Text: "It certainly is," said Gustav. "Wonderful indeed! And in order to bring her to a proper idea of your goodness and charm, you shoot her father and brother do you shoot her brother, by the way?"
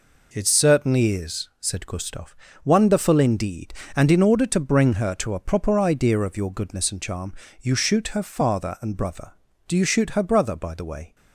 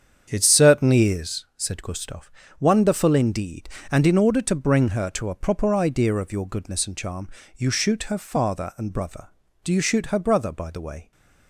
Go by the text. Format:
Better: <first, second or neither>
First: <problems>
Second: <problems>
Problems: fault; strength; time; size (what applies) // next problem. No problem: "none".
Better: first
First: none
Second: starts louder than the rest; strong; until 1.4 s; 7.5 dB